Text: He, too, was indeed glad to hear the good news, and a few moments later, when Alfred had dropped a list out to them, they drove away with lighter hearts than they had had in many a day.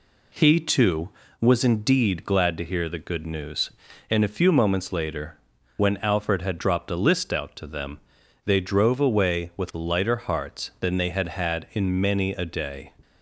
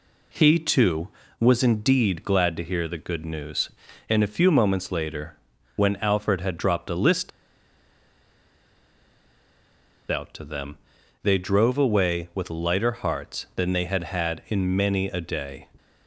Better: first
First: none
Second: pauses between "list" and "out"; strong; at 7.3 s; 2.8 s long

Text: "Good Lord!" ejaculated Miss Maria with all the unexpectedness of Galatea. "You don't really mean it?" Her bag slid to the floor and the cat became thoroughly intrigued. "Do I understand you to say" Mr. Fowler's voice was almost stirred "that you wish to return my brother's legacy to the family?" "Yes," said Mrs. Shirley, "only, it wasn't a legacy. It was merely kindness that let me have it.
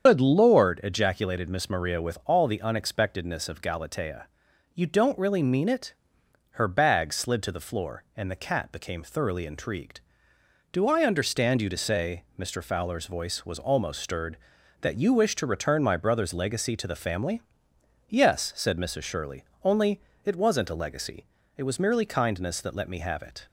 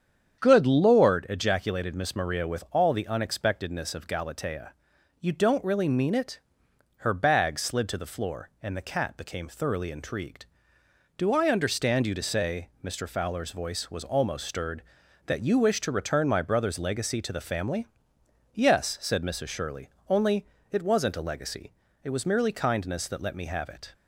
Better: second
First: loses the start of "Good"; at 0.0 s; 110 ms // starts louder than the rest; strong; until 1.0 s; 7.5 dB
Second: starts louder than the rest; strong; until 1.4 s; 8 dB

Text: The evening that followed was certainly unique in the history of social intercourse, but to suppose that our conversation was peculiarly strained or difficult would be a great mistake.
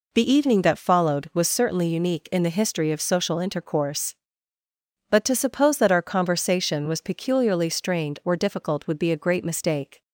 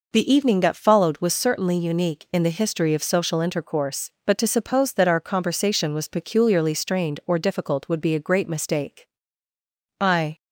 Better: first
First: none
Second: goes on to say "I"; slight; from 9.9 s on; 0.38 s long

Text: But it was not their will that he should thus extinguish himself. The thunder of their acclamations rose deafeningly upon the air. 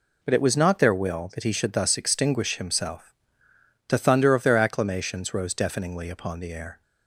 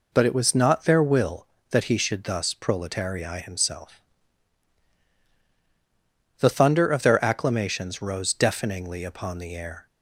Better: first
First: none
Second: says "proletarii" for "extinguish"; at 2.5 s

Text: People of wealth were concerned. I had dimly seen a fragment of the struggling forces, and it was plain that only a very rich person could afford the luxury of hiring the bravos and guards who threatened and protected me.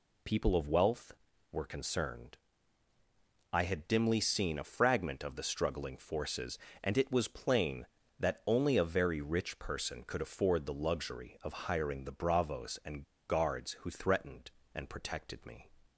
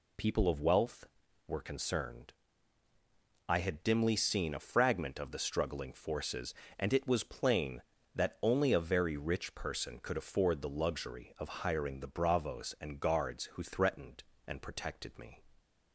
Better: second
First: pauses between "and" and "guards"; slight; at 13.0 s; 0.23 s long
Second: none

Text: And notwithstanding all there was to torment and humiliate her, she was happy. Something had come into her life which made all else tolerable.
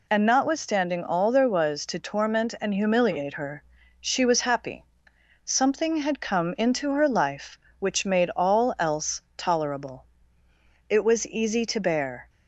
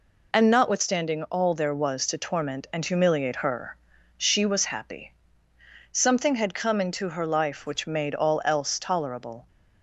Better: second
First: pauses between "else" and "tolerable"; slight; at 9.1 s; 0.16 s long // goes on to say "It was easy to bear"; from 10.8 s on; 1.4 s long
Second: none

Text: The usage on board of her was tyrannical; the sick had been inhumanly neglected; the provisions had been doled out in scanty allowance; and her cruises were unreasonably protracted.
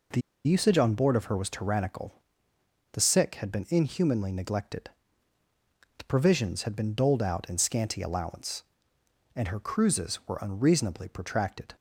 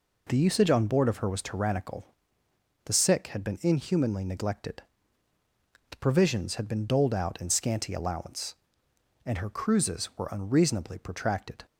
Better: second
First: pauses between "The" and "usage"; slight; at 0.2 s; 0.24 s long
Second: none

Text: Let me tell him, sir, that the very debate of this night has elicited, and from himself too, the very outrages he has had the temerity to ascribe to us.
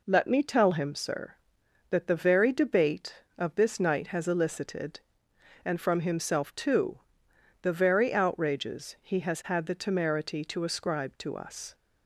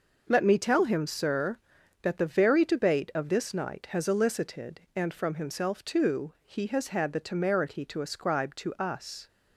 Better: first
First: none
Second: skips "the very outrages"; at 6.3 s

